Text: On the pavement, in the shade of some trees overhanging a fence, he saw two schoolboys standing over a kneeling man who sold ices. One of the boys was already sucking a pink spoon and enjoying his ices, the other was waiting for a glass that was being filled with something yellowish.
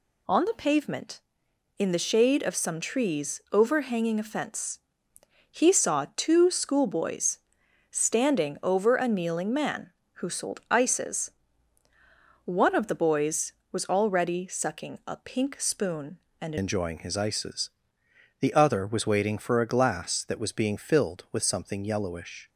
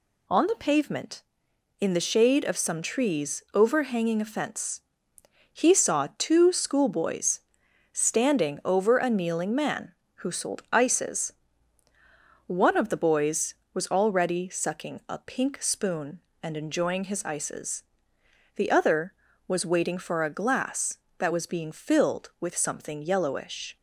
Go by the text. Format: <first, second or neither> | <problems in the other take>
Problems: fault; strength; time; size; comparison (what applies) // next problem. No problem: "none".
second | pauses between "schoolboys" and "standing"; noticeable; at 7.3 s; 0.54 s long; noticeable in the second // changes voice at "enjoying"; from 16.5 s on; 5.9 s long